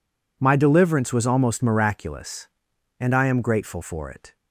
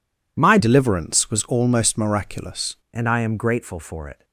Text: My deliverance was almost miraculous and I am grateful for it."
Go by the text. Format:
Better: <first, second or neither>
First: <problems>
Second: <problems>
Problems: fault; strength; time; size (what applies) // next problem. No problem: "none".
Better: first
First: none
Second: changes voice from "deliverance" to "miraculous"; from 0.5 to 2.7 s; 2.2 s long